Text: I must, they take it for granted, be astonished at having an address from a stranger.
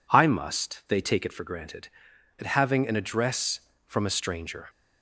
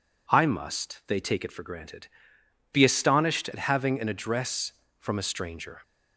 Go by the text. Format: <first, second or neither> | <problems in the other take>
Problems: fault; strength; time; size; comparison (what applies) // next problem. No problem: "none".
second | skips "be astonished"; at 2.1 s